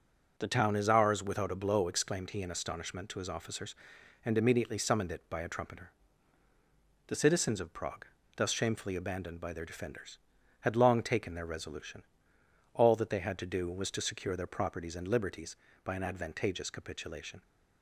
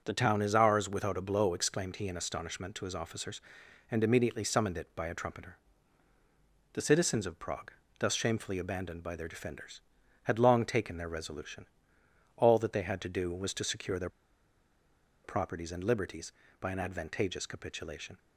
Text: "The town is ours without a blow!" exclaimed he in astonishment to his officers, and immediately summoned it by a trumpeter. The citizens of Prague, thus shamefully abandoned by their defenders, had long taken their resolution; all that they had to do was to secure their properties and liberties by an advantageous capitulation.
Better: first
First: starts louder than the rest; until 1.4 s; 6.5 dB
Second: starts louder than the rest; until 1.0 s; 6.5 dB // pauses between "their" and "properties"; at 14.0 s; 1.1 s long

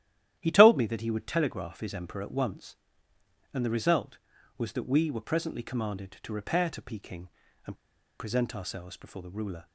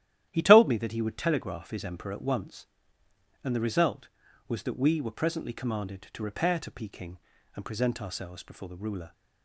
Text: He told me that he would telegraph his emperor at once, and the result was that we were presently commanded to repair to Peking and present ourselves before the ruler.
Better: second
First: starts louder than the rest; strong; until 1.3 s; 12 dB // pauses between "and" and "present"; at 7.7 s; 0.44 s long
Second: starts louder than the rest; strong; until 1.3 s; 12 dB

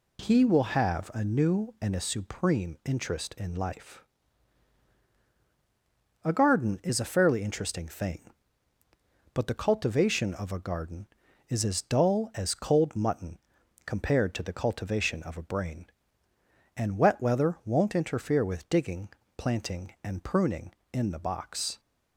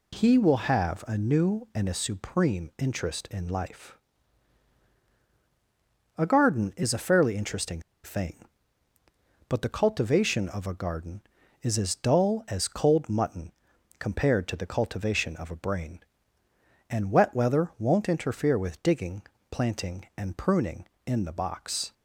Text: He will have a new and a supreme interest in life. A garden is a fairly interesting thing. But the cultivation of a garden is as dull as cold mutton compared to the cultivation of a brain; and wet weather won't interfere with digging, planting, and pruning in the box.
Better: first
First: pauses between "mutton" and "compared"; noticeable; at 13.3 s; 0.46 s long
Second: pauses between "interesting" and "thing"; slight; at 7.8 s; 0.22 s long // pauses between "mutton" and "compared"; noticeable; at 13.5 s; 0.46 s long

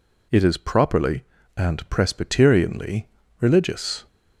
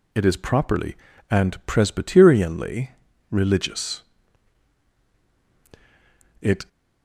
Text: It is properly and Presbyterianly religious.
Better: first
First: pauses between "Presbyterianly" and "religious"; slight; at 3.0 s; 0.36 s long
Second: pauses between "Presbyterianly" and "religious"; at 2.8 s; 0.40 s long // goes on to say "It"; slight; from 6.3 s on; 0.28 s long

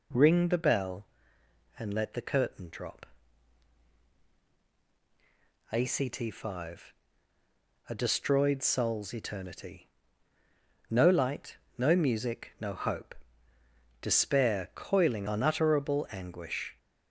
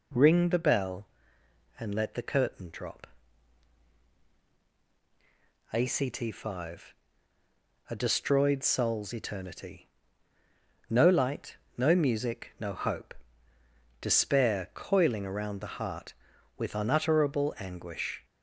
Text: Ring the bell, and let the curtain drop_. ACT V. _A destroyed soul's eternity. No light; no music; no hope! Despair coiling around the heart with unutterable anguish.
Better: second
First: skips "around the heart with"; at 15.2 s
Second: none

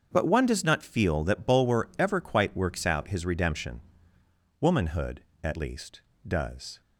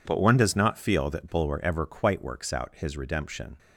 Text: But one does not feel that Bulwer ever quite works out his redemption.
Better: second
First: starts louder than the rest; until 1.1 s; 7 dB // goes on to say "Womanhood at least does"; strong; from 4.6 s on; 2.2 s long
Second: none

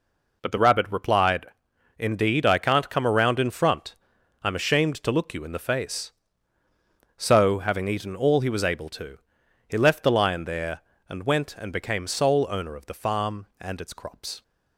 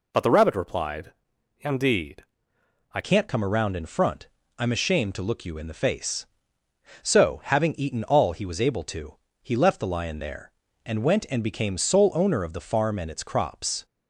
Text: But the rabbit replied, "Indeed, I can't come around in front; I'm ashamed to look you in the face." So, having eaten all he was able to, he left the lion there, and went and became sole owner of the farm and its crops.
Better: first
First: none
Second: changes voice at "can't"; from 3.0 s on; 10.8 s long

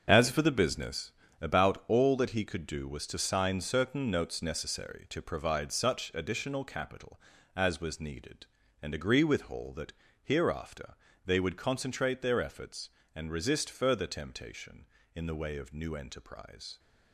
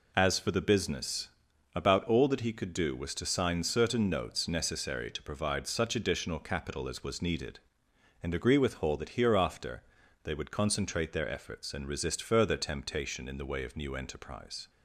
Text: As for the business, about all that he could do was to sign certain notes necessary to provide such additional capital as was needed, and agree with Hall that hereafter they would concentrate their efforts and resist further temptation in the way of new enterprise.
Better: second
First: gets quieter; strong; throughout; 9.5 dB // pauses between "that" and "hereafter"; slight; at 9.9 s; 0.30 s long // pauses between "hereafter" and "they"; slight; at 10.9 s; 0.32 s long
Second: pauses between "hereafter" and "they"; at 9.8 s; 0.42 s long

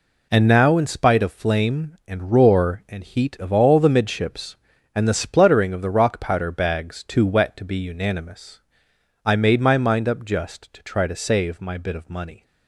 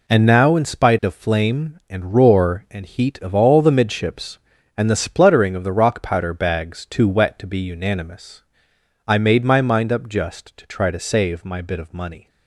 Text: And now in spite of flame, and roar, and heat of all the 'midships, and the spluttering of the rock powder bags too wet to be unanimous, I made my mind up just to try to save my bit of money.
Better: neither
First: none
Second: none

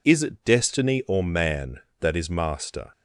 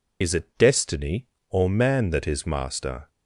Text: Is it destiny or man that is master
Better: first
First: none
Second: loses the start of "Is"; at 0.2 s; 40 ms

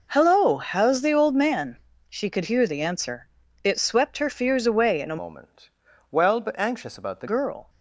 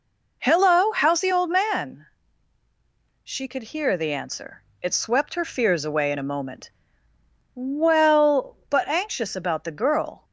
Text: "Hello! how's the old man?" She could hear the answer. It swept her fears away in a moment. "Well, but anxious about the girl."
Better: second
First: changes voice from "moment" to "the"; from 5.2 to 7.2 s; 2.0 s long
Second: none

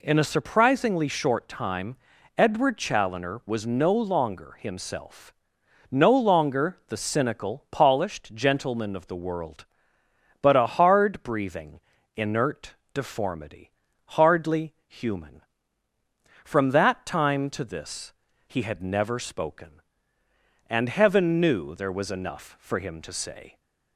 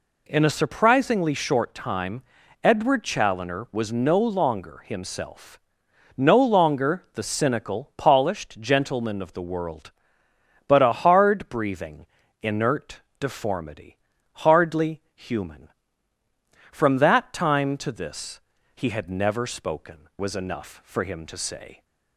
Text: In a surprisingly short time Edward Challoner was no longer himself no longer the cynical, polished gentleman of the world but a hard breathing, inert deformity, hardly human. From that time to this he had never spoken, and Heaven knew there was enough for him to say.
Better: first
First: pauses between "time" and "Edward"; at 1.9 s; 0.42 s long // pauses between "himself" and "no"; noticeable; at 5.3 s; 0.60 s long // pauses between "inert" and "deformity"; slight; at 12.7 s; 0.22 s long // pauses between "hardly" and "human"; slight; at 14.7 s; 0.16 s long // pauses between "this" and "he"; slight; at 18.1 s; 0.34 s long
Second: pauses between "time" and "Edward"; at 2.2 s; 0.42 s long // pauses between "himself" and "no"; noticeable; at 5.5 s; 0.60 s long // pauses between "inert" and "deformity"; slight; at 12.9 s; 0.22 s long // pauses between "hardly" and "human"; slight; at 14.9 s; 0.16 s long // pauses between "this" and "he"; slight; at 18.4 s; 0.34 s long // skips "and Heaven knew there"; at 20.1 s

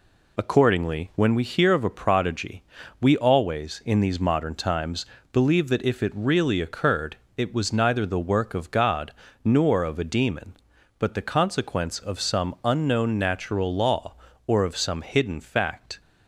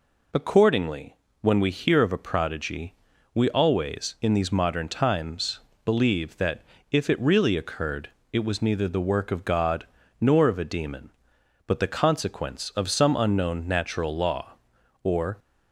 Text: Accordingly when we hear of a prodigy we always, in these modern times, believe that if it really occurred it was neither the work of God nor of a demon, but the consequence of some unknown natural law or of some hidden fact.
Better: first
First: pauses between "prodigy" and "we"; at 2.6 s; 0.38 s long // pauses between "occurred" and "it"; slight; at 7.1 s; 0.18 s long // pauses between "God" and "nor"; slight; at 9.1 s; 0.32 s long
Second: pauses between "Accordingly" and "when"; slight; at 1.1 s; 0.24 s long // pauses between "prodigy" and "we"; at 2.9 s; 0.38 s long // pauses between "that" and "if"; slight; at 6.6 s; 0.28 s long // pauses between "occurred" and "it"; slight; at 8.1 s; 0.20 s long // pauses between "God" and "nor"; slight; at 9.8 s; 0.34 s long // stops before "of some hidden fact"; at 15.3 s

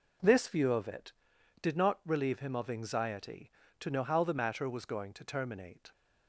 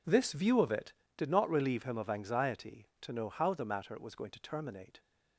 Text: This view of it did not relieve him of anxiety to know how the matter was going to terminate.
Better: neither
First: none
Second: none

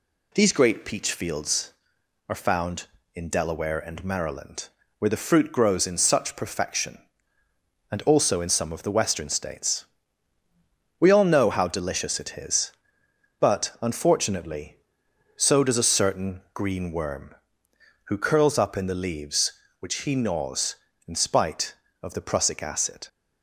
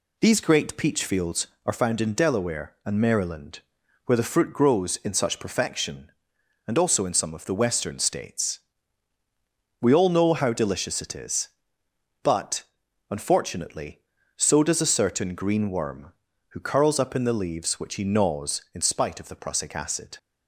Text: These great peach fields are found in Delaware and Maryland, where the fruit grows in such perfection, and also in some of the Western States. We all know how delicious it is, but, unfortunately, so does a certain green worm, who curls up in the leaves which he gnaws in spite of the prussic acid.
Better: neither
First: none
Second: none

